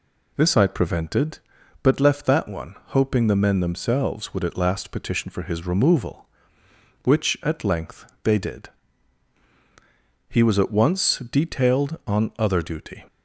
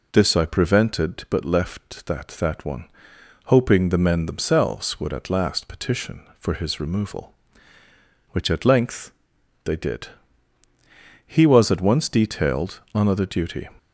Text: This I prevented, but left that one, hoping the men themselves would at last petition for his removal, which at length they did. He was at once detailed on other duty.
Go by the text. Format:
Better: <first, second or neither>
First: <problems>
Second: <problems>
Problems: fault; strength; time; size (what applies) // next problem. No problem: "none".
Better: first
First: pauses between "length" and "they"; slight; at 8.0 s; 0.16 s long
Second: says "that" twice; at 2.3 s // pauses between "length" and "they"; noticeable; at 9.1 s; 0.54 s long